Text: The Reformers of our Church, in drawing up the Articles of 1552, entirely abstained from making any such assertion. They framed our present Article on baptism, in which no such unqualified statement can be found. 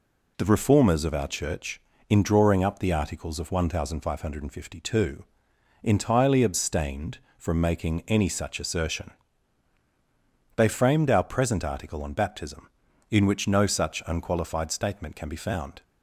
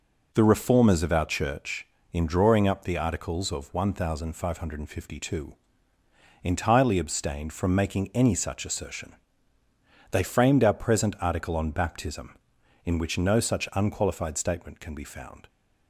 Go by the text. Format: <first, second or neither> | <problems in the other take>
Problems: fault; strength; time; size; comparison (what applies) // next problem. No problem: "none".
neither | none